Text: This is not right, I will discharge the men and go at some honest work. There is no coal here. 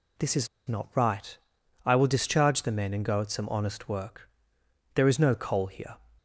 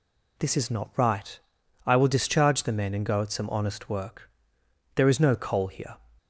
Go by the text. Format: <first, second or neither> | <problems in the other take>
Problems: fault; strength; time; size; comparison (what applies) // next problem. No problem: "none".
second | pauses between "is" and "not"; slight; at 0.4 s; 0.19 s long